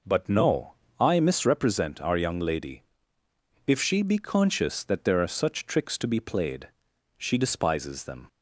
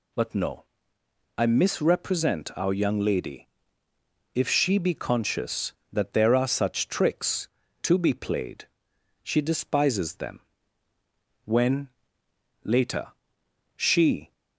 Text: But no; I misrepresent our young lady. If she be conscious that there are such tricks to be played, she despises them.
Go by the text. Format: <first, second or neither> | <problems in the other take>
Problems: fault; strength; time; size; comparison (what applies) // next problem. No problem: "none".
first | goes on to say "When later she"; strong; from 11.4 s on; 2.8 s long